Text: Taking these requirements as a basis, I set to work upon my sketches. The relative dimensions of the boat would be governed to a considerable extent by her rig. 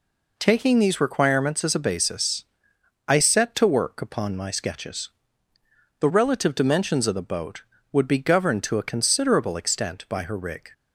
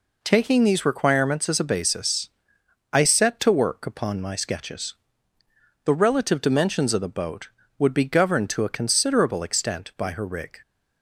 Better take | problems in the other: neither | none

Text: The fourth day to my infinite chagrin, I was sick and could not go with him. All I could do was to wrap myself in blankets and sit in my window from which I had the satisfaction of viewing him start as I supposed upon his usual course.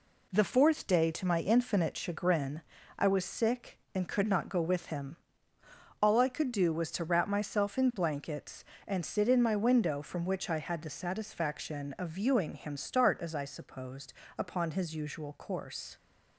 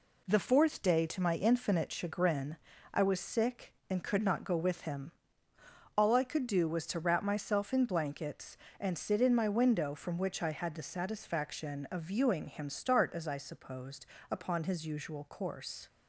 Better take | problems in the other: neither | pauses between "supposed" and "upon"; slight; the same in both

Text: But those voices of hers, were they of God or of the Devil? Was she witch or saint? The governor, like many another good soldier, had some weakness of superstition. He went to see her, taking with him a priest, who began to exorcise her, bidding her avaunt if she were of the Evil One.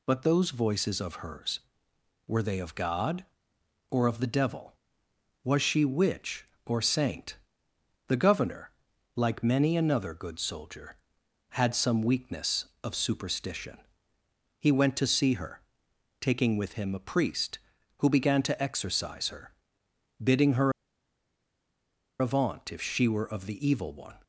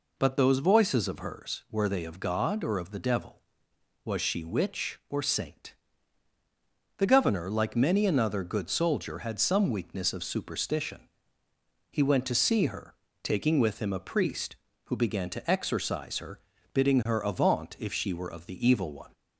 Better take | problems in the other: second | pauses between "her" and "avaunt"; strong; at 20.7 s; 1.4 s long

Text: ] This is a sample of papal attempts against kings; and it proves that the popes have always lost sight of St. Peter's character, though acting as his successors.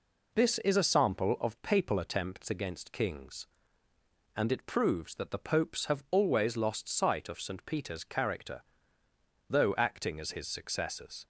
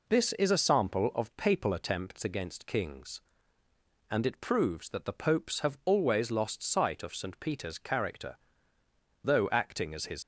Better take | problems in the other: first | stops before "successors"; at 10.2 s

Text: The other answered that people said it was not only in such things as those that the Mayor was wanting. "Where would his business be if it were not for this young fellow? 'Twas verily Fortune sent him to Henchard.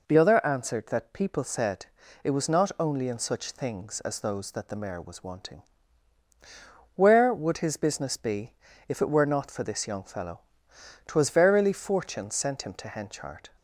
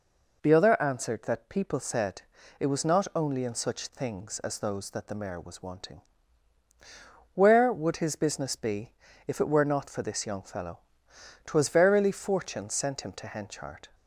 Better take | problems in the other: neither | pauses between "said" and "it"; the same in both // pauses between "be" and "if"; slight; the same in both

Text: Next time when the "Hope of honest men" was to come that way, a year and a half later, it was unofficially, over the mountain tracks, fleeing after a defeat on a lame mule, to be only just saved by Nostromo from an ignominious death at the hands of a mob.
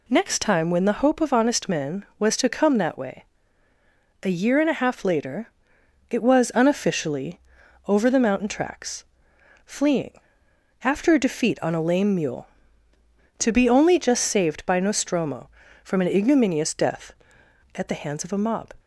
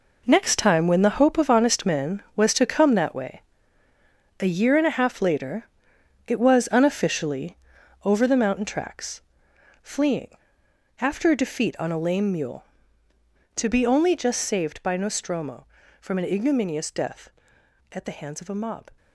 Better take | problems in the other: first | gets quieter; strong; throughout; 11 dB // pauses between "fleeing" and "after"; noticeable; at 10.2 s; 0.72 s long; noticeable in the first

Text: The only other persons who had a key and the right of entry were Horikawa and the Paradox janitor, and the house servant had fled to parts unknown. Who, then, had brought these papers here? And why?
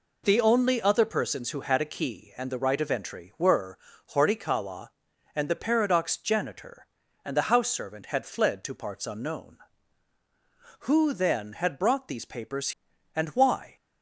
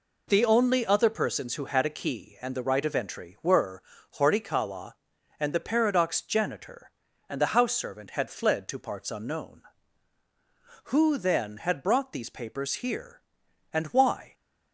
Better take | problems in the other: second | pauses between "were" and "Horikawa"; at 3.7 s; 0.38 s long; also in the second // skips "here"; at 12.9 s

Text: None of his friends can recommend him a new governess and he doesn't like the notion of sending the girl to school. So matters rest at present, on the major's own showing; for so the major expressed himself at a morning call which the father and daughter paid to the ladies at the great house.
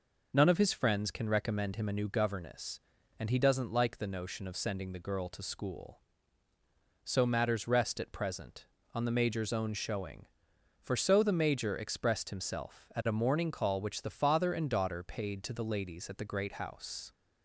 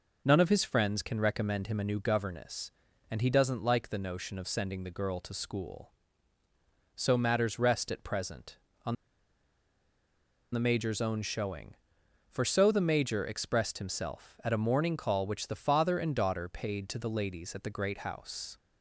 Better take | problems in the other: first | pauses between "on" and "the"; strong; at 8.9 s; 1.5 s long

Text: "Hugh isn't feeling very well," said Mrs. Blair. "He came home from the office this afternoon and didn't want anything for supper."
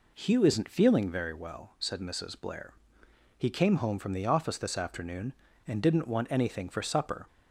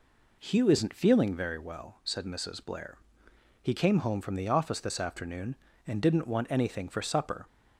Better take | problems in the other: neither | none

